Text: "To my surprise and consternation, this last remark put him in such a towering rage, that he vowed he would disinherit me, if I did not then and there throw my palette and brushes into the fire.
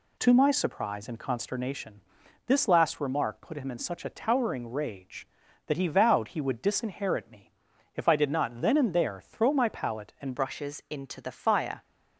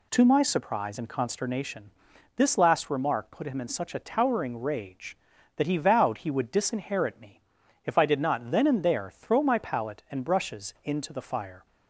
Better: second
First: changes voice at "brushes"; from 10.3 s on; 1.5 s long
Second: none

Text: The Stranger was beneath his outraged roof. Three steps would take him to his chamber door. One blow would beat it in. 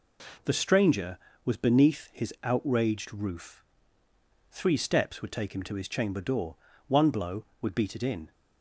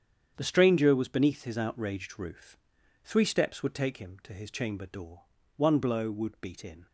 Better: first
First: none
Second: starts louder than the rest; strong; until 1.3 s; 8 dB // skips "it"; at 6.6 s

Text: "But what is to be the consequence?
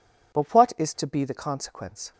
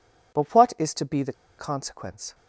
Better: first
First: none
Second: pauses between "the" and "consequence"; slight; at 1.3 s; 0.25 s long

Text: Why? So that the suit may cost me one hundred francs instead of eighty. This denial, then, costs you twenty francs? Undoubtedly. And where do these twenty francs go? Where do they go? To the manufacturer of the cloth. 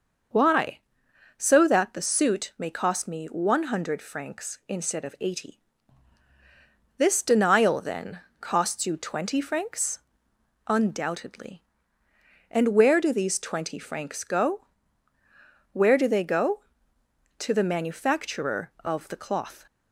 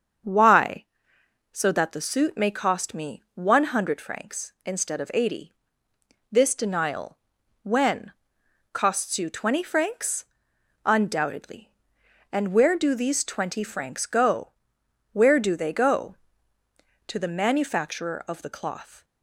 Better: first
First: starts louder than the rest; noticeable; until 1.9 s; 6 dB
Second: starts louder than the rest; strong; until 1.9 s; 7 dB // says "when" for "then"; at 7.6 s

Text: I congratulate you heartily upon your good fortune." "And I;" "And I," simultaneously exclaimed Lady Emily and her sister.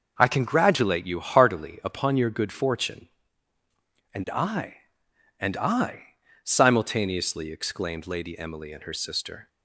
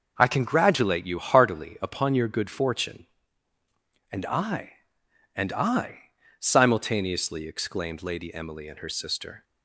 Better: neither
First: none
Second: none

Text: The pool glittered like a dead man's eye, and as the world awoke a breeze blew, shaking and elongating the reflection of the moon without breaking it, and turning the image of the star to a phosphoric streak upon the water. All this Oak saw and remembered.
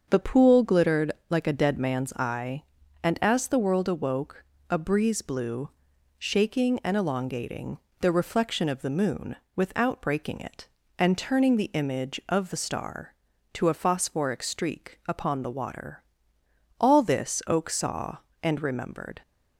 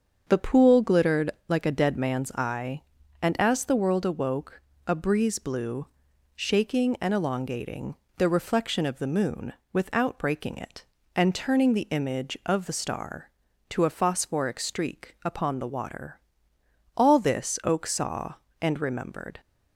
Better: neither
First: starts louder than the rest; until 1.0 s; 6.5 dB // pauses between "glittered" and "like"; slight; at 1.1 s; 0.18 s long // pauses between "awoke" and "a"; slight; at 4.4 s; 0.28 s long // pauses between "elongating" and "the"; slight; at 7.7 s; 0.24 s long // pauses between "moon" and "without"; slight; at 9.3 s; 0.20 s long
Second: starts louder than the rest; until 1.2 s; 6.5 dB // pauses between "glittered" and "like"; slight; at 1.2 s; 0.18 s long // pauses between "awoke" and "a"; slight; at 4.5 s; 0.28 s long // pauses between "elongating" and "the"; slight; at 7.9 s; 0.24 s long // pauses between "moon" and "without"; slight; at 9.5 s; 0.20 s long

